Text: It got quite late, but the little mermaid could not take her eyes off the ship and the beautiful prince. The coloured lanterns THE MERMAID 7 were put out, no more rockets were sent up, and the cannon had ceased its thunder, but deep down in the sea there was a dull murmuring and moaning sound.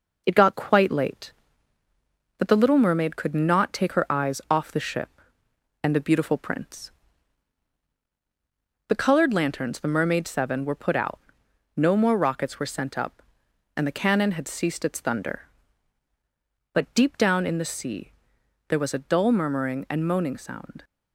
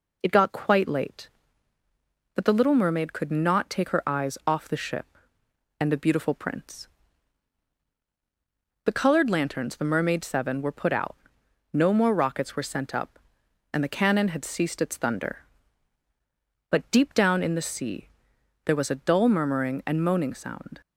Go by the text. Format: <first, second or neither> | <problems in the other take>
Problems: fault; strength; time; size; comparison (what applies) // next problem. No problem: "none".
second | gets quieter; throughout; 3.5 dB // pauses between "sea" and "there"; noticeable; at 18.1 s; 0.58 s long; noticeable in the second